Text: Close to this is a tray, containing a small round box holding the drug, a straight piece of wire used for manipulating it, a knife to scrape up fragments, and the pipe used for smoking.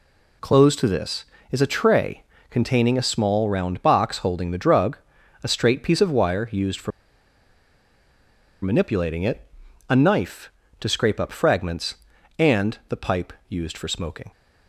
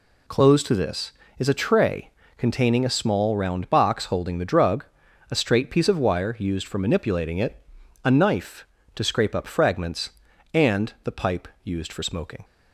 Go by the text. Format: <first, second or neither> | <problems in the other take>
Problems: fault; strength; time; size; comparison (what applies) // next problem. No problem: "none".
second | pauses between "for" and "manipulating"; strong; at 6.9 s; 1.7 s long // pauses between "pipe" and "used"; slight; at 13.3 s; 0.16 s long; slight in the second